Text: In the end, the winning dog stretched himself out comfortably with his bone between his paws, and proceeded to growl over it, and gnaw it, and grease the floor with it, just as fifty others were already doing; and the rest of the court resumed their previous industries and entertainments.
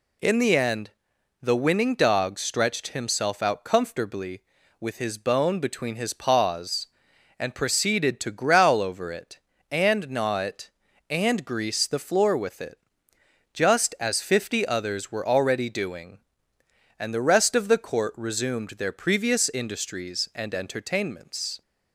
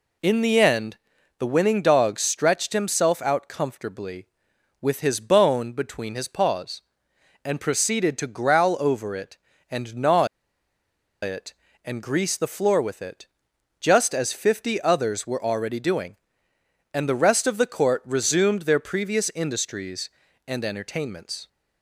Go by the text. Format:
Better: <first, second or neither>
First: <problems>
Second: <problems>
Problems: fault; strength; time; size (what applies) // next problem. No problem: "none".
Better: first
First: none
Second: pauses between "gnaw" and "it"; noticeable; at 10.2 s; 0.97 s long